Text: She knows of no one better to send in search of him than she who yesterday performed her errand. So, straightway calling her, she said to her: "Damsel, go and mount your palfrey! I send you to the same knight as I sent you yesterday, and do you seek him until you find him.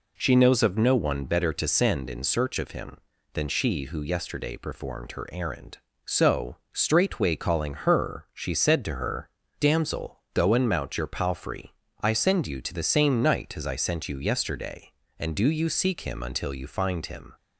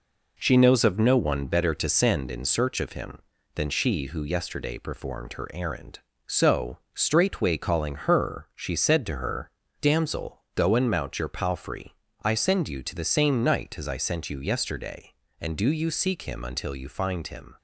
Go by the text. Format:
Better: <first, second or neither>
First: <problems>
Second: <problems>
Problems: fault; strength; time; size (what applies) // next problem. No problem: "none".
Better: first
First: none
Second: gets quieter; noticeable; throughout; 5 dB